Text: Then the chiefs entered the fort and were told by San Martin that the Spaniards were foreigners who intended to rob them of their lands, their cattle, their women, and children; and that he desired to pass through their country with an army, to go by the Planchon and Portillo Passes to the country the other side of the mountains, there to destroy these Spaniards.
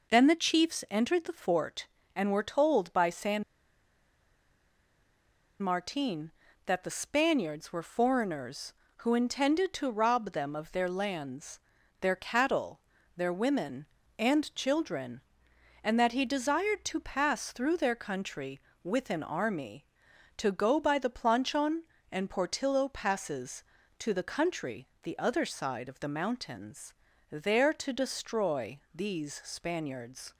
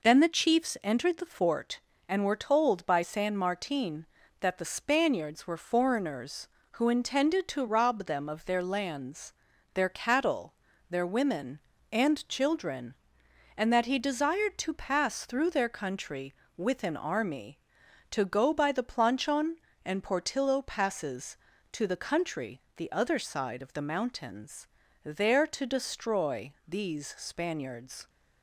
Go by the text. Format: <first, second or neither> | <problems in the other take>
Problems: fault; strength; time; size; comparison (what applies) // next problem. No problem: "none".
second | pauses between "San" and "Martin"; strong; at 3.4 s; 2.1 s long